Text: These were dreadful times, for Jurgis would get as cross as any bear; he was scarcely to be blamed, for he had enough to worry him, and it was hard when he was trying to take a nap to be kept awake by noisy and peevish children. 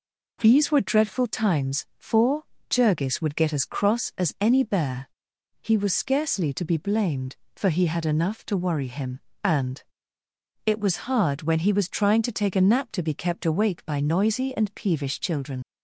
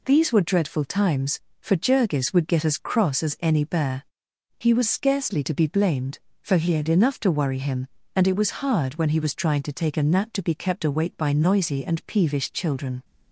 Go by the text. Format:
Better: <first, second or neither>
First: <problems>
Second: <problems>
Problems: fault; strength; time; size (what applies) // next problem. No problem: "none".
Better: second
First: pauses between "for" and "Jurgis"; slight; at 2.4 s; 0.26 s long // pauses between "and" and "it"; noticeable; at 9.8 s; 0.82 s long // leaves "children" unfinished; at 15.6 s; 70 ms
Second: none